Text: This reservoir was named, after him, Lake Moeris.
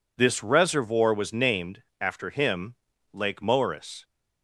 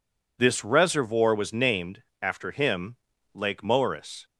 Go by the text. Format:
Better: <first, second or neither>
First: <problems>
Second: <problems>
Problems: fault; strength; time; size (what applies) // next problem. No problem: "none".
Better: neither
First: none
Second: none